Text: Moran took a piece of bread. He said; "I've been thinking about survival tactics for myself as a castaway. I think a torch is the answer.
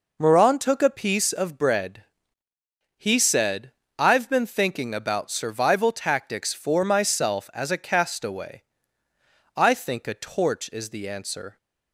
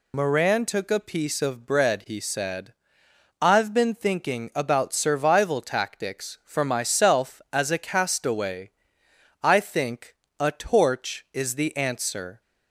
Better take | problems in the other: first | loses the start of "Moran"; at 0.1 s; 45 ms // pauses between "think" and "a"; slight; at 10.1 s; 0.26 s long

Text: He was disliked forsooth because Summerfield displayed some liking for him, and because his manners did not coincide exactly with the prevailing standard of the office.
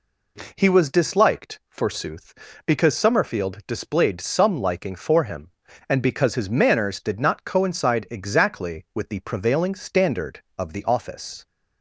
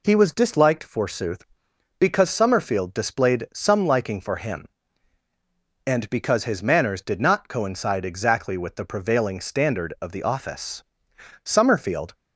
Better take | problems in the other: first | goes on to say "Summerfield"; noticeable; from 11.4 s on; 0.70 s long

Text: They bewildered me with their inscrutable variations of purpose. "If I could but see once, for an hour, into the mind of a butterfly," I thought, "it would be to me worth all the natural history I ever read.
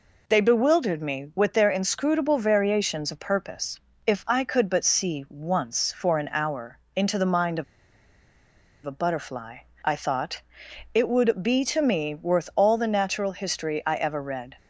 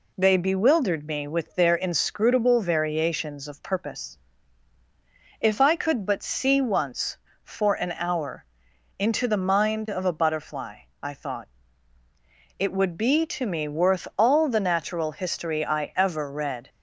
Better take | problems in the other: second | pauses between "of" and "a"; at 7.6 s; 1.2 s long

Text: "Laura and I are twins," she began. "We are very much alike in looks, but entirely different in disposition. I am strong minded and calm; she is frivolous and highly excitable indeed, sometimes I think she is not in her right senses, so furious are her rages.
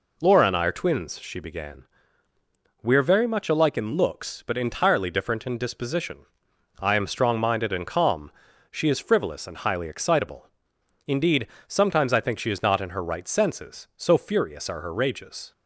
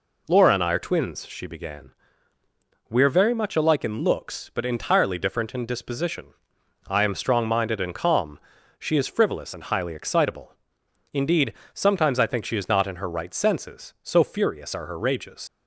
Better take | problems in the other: first | pauses between "excitable" and "indeed"; noticeable; at 10.5 s; 0.58 s long; noticeable in the first // leaves "rages" unfinished; at 15.4 s; 100 ms

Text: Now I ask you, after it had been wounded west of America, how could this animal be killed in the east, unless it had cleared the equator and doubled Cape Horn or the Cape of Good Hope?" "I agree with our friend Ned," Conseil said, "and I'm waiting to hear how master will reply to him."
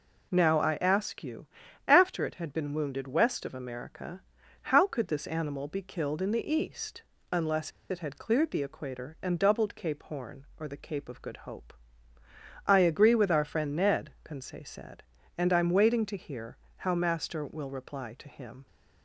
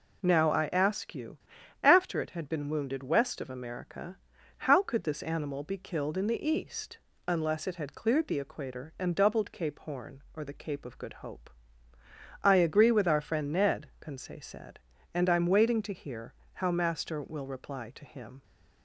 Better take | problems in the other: second | pauses between "unless" and "it"; slight; at 7.7 s; 0.19 s long // pauses between "hear" and "how"; slight; at 16.5 s; 0.18 s long; slight in the second

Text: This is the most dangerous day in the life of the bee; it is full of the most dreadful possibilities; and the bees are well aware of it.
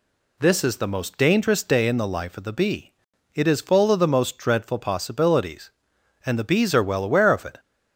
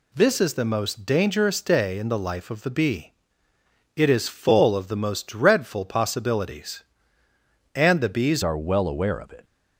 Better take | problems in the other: first | changes voice at "are"; from 8.4 s on; 1.0 s long

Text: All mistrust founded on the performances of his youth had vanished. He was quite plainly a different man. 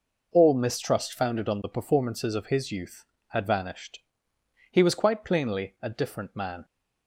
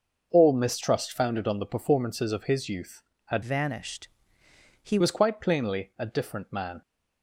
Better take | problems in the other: first | starts louder than the rest; noticeable; until 1.3 s; 6 dB // changes voice from "vanished" to "He"; from 3.4 to 4.9 s; 1.5 s long

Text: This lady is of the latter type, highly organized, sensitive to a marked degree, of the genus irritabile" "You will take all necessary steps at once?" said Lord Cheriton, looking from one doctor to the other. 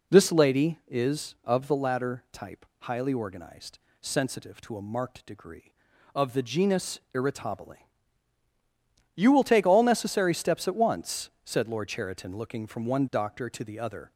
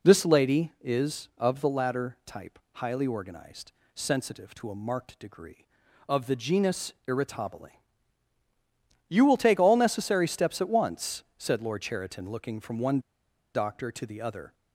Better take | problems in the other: first | pauses between "irritabile" and "You"; strong; at 7.6 s; 1.4 s long; strong in the first // pauses between "one" and "doctor"; noticeable; at 12.9 s; 0.55 s long

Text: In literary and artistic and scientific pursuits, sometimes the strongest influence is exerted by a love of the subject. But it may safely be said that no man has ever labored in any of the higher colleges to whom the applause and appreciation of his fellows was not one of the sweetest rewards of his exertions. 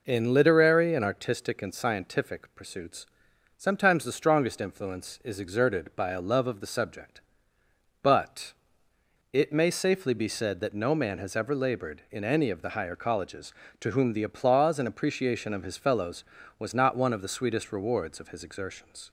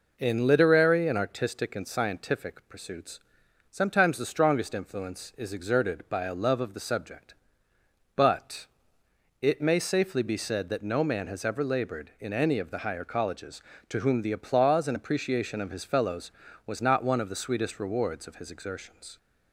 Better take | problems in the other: neither | pauses between "But" and "it"; noticeable; the same in both

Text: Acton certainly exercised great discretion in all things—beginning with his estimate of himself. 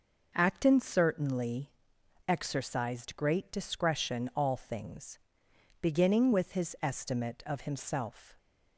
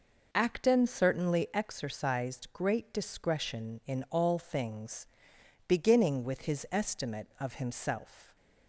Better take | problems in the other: second | pauses between "certainly" and "exercised"; noticeable; at 1.6 s; 0.58 s long // skips "in"; at 4.3 s

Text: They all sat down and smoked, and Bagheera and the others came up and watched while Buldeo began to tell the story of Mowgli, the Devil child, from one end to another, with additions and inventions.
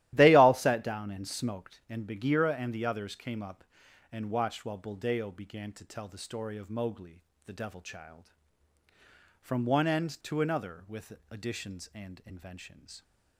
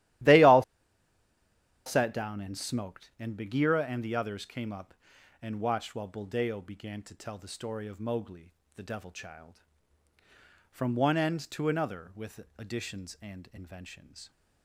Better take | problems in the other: first | starts louder than the rest; strong; until 2.4 s; 14 dB; strong in the first // pauses between "all" and "sat"; at 0.6 s; 1.2 s long // pauses between "with" and "additions"; slight; at 12.3 s; 0.16 s long; slight in the first

